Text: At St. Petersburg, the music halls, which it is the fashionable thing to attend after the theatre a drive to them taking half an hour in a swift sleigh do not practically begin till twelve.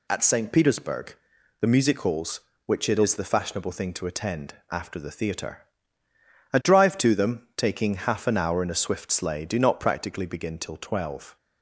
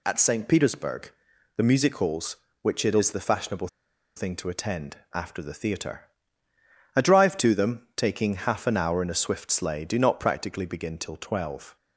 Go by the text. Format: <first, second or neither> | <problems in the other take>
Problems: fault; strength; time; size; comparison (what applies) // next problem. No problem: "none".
first | pauses between "fashionable" and "thing"; noticeable; at 3.6 s; 0.48 s long // pauses between "attend" and "after"; slight; at 4.9 s; 0.18 s long; slight in the first // pauses between "theatre" and "a"; noticeable; at 6.0 s; 0.96 s long; noticeable in the first